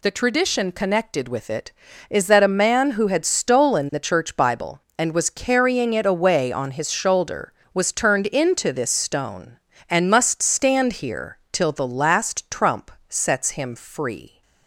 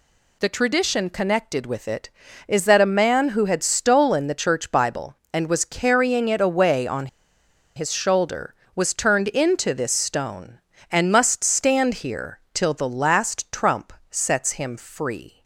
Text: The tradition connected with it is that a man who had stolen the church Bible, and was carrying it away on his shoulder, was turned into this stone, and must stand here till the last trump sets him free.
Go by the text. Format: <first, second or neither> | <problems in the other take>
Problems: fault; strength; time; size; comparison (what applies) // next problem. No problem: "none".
first | pauses between "on" and "his"; noticeable; at 7.0 s; 0.69 s long // pauses between "trump" and "sets"; slight; at 13.9 s; 0.18 s long; slight in the first